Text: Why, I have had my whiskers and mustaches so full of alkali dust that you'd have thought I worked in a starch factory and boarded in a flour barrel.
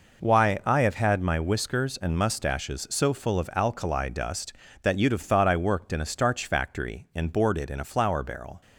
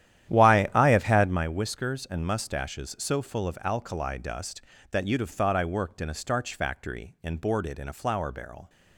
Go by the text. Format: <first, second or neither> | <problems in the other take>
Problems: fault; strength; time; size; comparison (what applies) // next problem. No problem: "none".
first | starts louder than the rest; strong; until 1.5 s; 11.5 dB